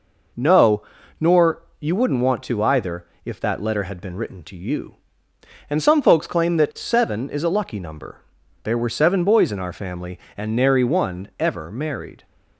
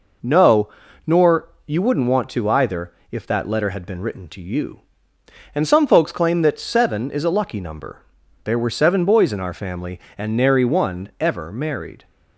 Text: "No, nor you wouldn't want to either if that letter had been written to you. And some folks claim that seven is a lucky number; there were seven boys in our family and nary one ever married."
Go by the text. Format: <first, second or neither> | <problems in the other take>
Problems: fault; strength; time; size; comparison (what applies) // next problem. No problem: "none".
neither | pauses between "nor" and "you"; slight; the same in both // pauses between "either" and "if"; slight; the same in both